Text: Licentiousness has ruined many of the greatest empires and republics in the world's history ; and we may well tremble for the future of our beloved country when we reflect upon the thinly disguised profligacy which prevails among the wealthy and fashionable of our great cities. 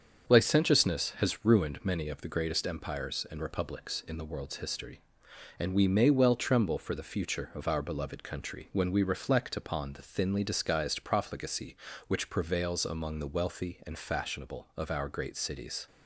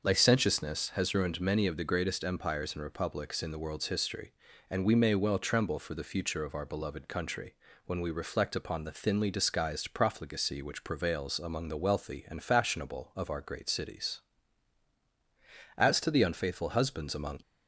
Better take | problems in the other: first | starts louder than the rest; noticeable; until 1.0 s; 6 dB; also in the first // pauses between "country" and "when"; slight; at 7.5 s; 0.32 s long // goes on to say "As to the unfaithful husbands among"; from 15.7 s on; 1.6 s long

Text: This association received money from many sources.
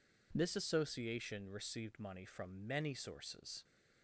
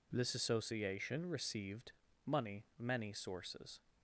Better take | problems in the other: first | pauses between "received" and "money"; slight; at 1.9 s; 0.34 s long // skips "from"; at 2.7 s

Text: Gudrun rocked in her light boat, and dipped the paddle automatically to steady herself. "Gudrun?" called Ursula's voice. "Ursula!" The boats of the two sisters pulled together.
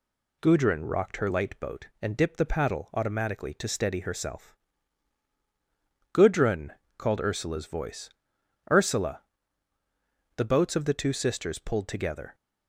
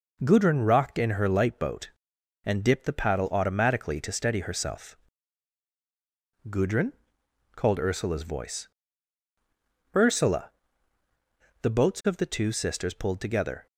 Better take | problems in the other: second | skips "in"; at 1.1 s

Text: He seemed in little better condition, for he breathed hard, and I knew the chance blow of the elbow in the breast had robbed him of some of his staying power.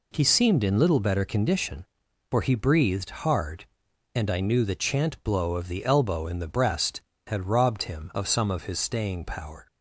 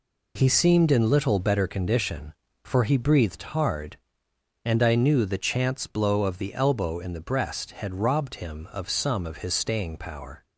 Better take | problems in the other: second | says "chant" for "chance"; at 4.7 s

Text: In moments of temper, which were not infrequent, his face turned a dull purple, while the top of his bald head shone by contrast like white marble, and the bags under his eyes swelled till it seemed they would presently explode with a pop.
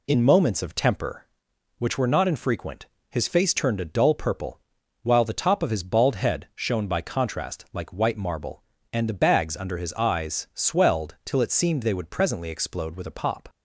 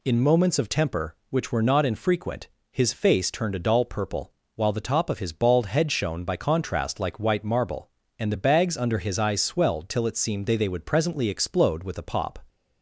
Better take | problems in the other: first | says "they" twice; at 10.5 s

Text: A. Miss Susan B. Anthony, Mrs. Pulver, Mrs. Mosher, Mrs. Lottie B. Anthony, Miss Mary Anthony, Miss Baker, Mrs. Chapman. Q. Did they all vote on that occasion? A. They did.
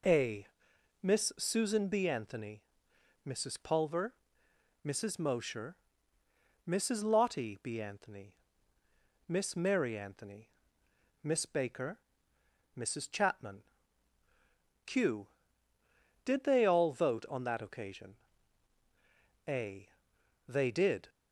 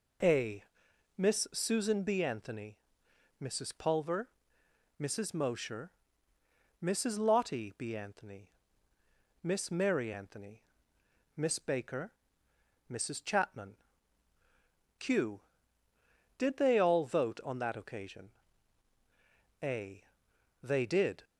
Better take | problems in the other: neither | none

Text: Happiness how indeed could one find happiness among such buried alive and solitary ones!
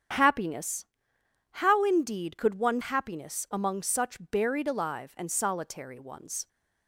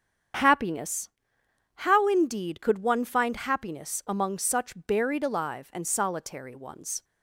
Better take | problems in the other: second | starts louder than the rest; strong; until 1.8 s; 8 dB; strong in the second // pauses between "Happiness" and "how"; noticeable; at 0.8 s; 0.68 s long; noticeable in the second // skips "find"; at 2.8 s

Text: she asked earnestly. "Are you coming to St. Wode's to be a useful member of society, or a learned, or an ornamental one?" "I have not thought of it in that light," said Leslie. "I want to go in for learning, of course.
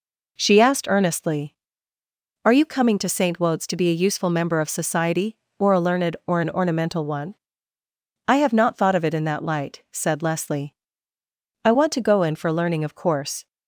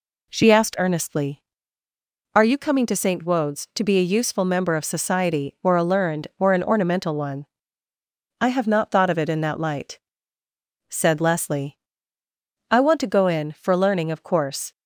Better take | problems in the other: neither | none

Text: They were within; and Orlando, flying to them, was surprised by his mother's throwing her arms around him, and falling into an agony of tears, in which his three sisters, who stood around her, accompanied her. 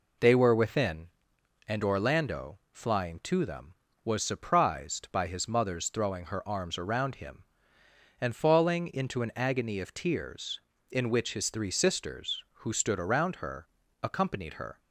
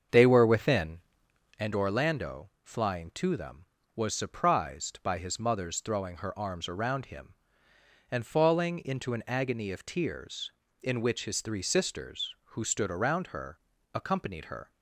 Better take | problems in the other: first | starts louder than the rest; until 1.7 s; 7 dB

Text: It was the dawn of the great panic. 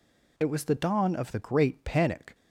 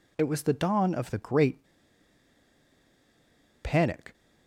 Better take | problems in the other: first | pauses between "great" and "panic"; strong; at 1.6 s; 1.9 s long

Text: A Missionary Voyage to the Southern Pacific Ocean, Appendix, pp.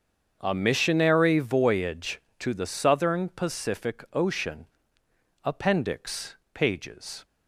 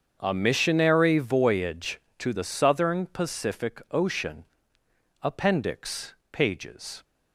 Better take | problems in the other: neither | starts louder than the rest; the same in both

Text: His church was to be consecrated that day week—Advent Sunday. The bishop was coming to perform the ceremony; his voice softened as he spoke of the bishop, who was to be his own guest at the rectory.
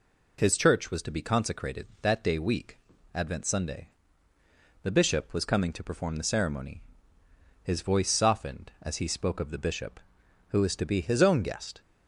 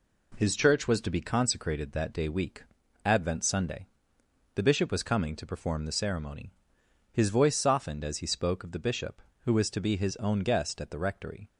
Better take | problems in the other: second | stops before "at the rectory"; at 11.8 s

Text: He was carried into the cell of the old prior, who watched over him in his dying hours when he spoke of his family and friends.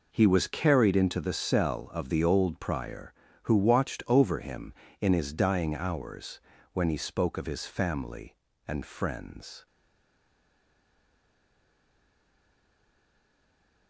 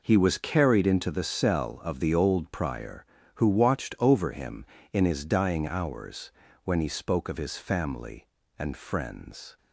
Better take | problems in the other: second | pauses between "hours" and "when"; slight; at 6.3 s; 0.34 s long; slight in the second // stays silent after the last word; strong; from 9.6 s on; 4.2 s long

